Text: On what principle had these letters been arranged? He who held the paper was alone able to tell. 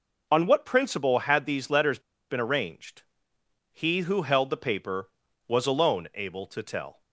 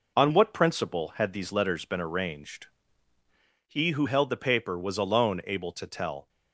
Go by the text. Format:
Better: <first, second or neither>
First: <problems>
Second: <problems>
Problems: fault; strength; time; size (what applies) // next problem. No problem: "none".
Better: second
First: pauses between "letters" and "been"; slight; at 1.9 s; 0.30 s long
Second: none